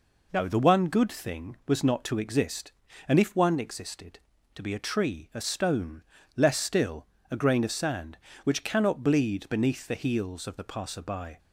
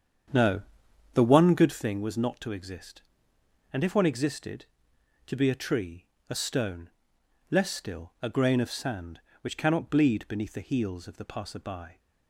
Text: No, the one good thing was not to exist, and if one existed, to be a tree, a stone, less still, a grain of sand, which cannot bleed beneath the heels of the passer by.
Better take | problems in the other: first | starts louder than the rest; strong; until 1.8 s; 8 dB

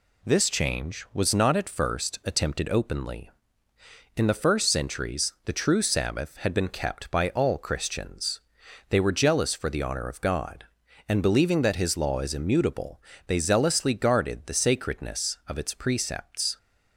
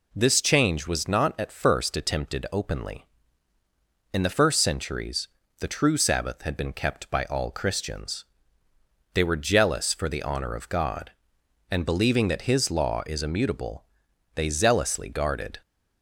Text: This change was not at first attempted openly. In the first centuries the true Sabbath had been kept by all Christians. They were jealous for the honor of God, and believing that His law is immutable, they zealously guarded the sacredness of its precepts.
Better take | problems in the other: first | pauses between "centuries" and "the"; slight; at 5.2 s; 0.30 s long // stops before "the sacredness of its precepts"; at 15.6 s

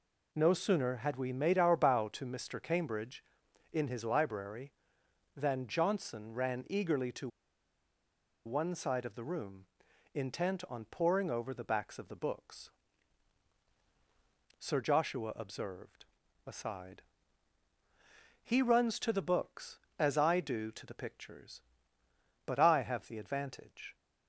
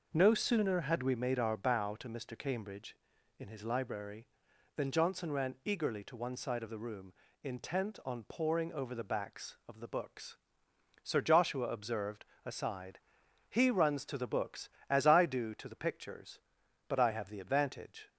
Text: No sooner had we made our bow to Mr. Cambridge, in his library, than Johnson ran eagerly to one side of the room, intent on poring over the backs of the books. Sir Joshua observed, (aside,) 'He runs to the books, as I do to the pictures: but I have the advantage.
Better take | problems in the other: second | pauses between "to" and "one"; at 7.2 s; 1.1 s long

